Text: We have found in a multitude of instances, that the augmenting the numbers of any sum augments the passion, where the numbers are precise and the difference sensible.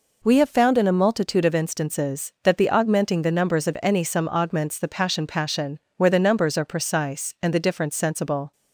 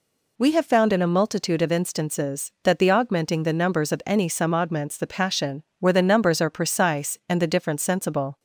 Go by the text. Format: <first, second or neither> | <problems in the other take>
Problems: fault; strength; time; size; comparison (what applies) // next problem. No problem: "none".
second | says "passion" twice; at 5.2 s